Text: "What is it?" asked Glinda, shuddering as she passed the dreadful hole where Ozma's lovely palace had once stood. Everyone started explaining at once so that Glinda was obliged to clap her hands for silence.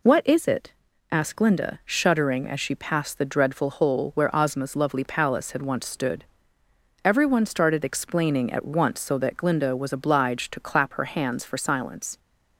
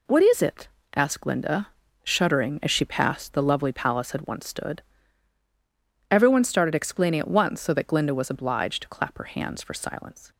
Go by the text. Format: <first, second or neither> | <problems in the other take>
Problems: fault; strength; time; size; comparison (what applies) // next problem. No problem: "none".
first | skips "dreadful hole where Ozma's"; at 3.4 s